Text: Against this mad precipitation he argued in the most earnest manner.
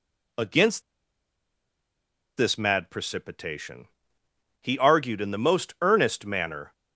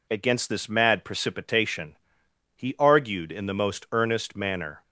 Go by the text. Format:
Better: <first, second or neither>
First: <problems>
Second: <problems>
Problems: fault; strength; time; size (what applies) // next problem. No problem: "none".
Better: second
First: pauses between "Against" and "this"; strong; at 0.8 s; 1.5 s long // pauses between "precipitation" and "he"; noticeable; at 3.8 s; 0.74 s long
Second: pauses between "precipitation" and "he"; noticeable; at 1.9 s; 0.62 s long